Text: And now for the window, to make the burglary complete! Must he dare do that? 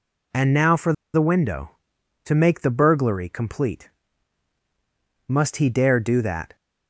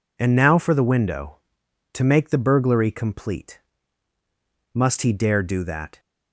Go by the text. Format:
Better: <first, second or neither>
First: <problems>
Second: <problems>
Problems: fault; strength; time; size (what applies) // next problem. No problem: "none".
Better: second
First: pauses between "for" and "the"; slight; at 0.9 s; 0.21 s long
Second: none